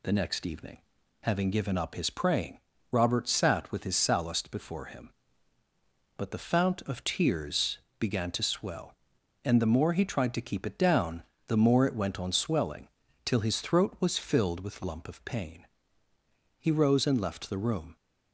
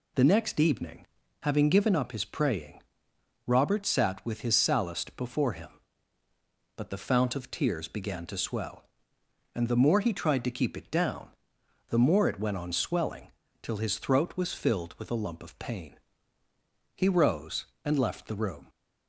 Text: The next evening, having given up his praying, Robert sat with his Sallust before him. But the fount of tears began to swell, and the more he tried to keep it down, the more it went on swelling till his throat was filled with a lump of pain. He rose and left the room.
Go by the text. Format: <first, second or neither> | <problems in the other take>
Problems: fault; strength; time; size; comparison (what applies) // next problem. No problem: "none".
second | pauses between "tears" and "began"; slight; at 7.7 s; 0.20 s long // pauses between "swelling" and "till"; at 12.8 s; 0.38 s long; slight in the second // skips "a"; at 14.8 s